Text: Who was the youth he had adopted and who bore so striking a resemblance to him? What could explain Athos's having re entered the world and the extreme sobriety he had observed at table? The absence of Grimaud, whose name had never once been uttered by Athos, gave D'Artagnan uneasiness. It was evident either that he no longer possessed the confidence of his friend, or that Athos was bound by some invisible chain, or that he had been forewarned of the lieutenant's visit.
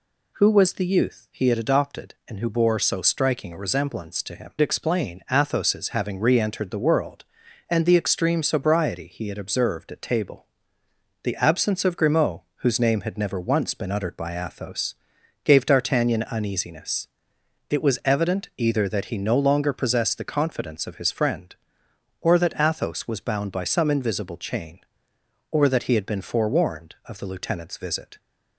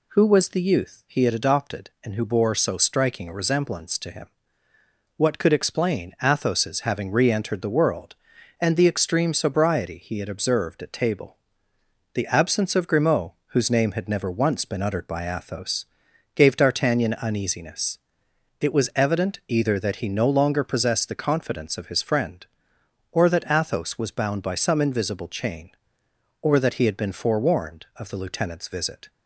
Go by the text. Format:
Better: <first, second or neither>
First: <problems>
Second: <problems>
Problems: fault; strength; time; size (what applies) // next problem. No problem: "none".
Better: second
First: skips "What could"; at 4.5 s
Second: none